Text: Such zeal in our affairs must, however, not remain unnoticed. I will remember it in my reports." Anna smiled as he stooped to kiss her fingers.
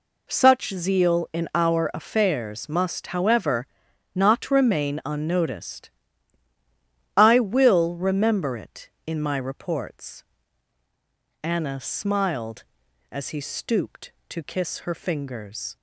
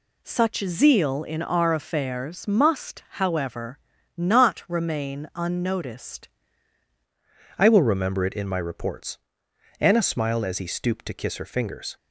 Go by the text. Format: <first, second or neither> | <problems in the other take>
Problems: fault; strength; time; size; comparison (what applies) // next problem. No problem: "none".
first | changes voice at "I"; from 7.5 s on; 4.4 s long